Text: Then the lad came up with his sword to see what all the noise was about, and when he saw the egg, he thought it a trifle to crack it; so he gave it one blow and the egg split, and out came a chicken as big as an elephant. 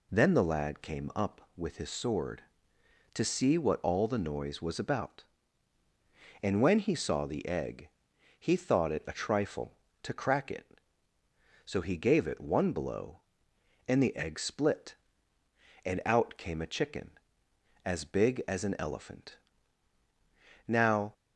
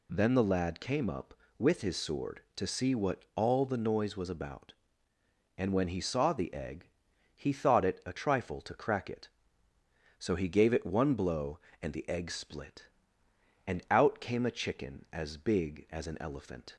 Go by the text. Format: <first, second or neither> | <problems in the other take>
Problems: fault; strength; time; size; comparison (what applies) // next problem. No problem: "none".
second | goes on to say "Now"; slight; from 20.6 s on; 0.46 s long